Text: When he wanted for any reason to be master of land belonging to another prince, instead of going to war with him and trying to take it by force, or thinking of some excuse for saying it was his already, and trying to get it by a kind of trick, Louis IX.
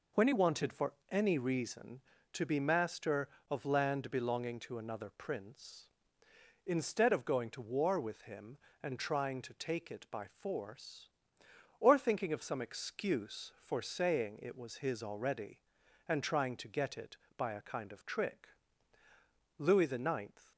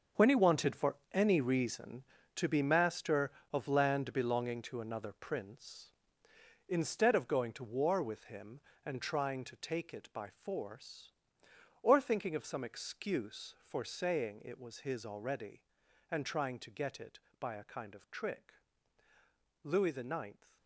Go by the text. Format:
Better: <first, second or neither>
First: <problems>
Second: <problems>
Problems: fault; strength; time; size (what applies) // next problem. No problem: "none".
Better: first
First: pauses between "for" and "any"; slight; at 0.9 s; 0.16 s long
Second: gets quieter; strong; throughout; 12 dB // pauses between "for" and "any"; slight; at 0.9 s; 0.16 s long